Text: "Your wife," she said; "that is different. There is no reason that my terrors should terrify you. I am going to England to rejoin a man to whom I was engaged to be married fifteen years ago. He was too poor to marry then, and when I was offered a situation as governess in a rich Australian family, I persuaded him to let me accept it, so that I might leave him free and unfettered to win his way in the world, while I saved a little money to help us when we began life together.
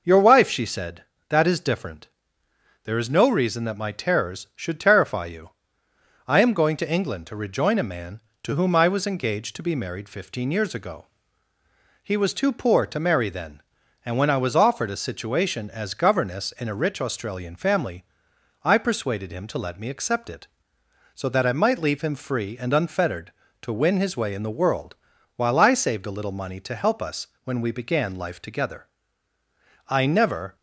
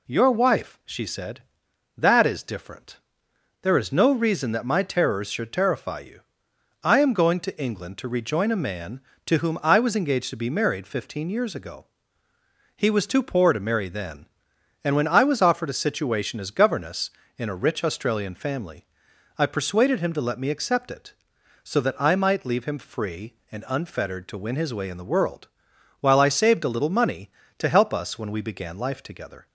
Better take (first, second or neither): second